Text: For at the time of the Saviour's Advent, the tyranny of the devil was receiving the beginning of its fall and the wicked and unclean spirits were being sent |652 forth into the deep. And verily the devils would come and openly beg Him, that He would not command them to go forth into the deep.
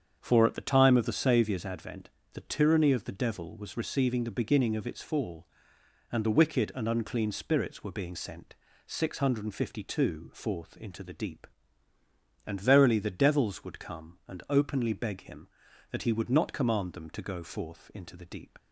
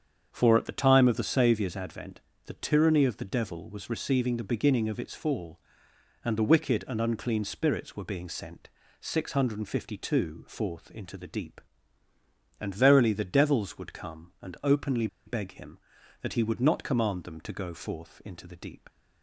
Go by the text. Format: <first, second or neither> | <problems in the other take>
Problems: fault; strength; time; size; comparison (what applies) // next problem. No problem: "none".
first | starts louder than the rest; strong; until 1.3 s; 7.5 dB; strong in the first // pauses between "openly" and "beg"; slight; at 15.0 s; 0.18 s long